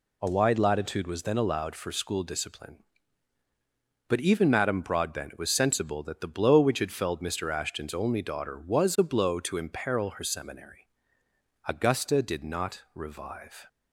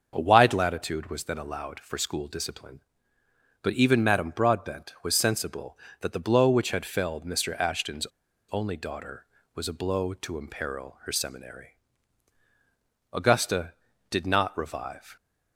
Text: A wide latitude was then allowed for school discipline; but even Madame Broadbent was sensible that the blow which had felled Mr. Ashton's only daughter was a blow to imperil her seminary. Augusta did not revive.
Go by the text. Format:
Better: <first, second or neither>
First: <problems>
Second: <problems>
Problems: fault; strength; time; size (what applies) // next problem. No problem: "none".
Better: first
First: none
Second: starts louder than the rest; until 1.1 s; 6.5 dB // pauses between "Ashton's" and "only"; at 8.0 s; 0.45 s long